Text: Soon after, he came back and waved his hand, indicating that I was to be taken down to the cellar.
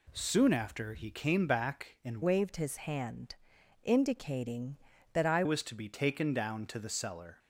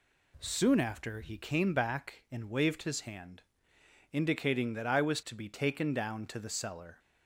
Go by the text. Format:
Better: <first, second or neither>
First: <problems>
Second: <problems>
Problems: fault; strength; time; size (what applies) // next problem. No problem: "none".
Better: second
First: changes voice from "waved" to "I"; from 2.2 to 5.4 s; 3.2 s long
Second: none